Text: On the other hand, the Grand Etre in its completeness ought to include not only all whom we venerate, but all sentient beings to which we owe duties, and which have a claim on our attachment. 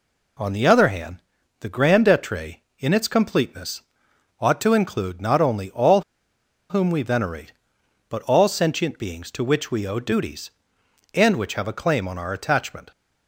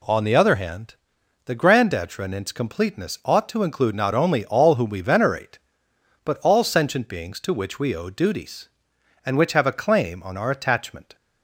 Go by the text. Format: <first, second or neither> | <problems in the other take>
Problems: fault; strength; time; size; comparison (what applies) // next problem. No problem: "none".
second | pauses between "completeness" and "ought"; noticeable; at 3.8 s; 0.58 s long // pauses between "all" and "whom"; noticeable; at 6.0 s; 0.68 s long